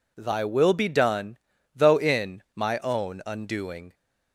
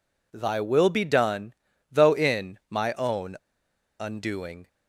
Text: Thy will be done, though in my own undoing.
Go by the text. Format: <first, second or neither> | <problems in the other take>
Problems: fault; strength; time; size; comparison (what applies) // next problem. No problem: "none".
first | pauses between "own" and "undoing"; noticeable; at 3.3 s; 0.65 s long